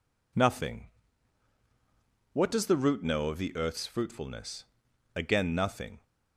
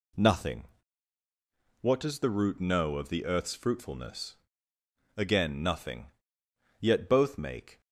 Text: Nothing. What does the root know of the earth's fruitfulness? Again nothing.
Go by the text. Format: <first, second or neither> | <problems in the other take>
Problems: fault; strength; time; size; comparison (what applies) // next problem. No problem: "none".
first | goes on to say "Yet both make"; noticeable; from 6.7 s on; 1.0 s long